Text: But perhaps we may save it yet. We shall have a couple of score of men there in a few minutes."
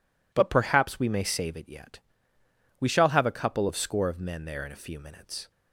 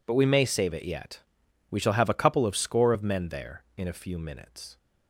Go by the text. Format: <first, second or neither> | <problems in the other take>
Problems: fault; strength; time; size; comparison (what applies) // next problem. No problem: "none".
first | skips "perhaps"; at 0.1 s